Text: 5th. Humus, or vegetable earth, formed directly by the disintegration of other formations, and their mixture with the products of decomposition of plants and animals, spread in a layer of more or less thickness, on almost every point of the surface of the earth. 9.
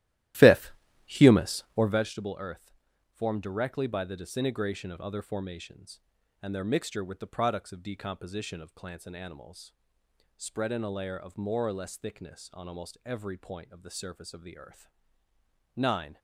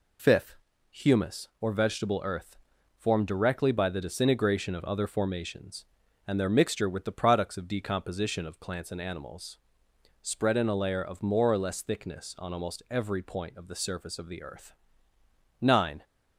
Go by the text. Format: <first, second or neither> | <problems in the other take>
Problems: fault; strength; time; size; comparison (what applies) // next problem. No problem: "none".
second | starts louder than the rest; strong; until 2.1 s; 14.5 dB